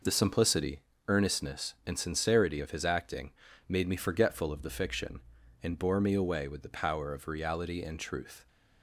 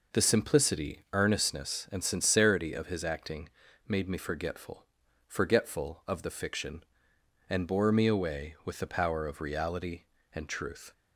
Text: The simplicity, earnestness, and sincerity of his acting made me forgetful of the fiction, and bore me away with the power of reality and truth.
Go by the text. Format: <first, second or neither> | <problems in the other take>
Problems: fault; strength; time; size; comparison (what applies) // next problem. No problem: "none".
first | pauses between "acting" and "made"; at 3.4 s; 0.38 s long; slight in the first // says "forgetful" twice; at 5.2 s